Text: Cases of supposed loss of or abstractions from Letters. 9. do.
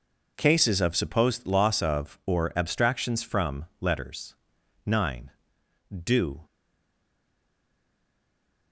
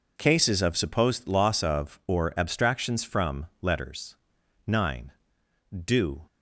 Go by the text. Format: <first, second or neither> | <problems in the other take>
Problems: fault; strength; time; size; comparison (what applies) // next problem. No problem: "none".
second | stays silent after the last word; from 6.4 s on; 2.3 s long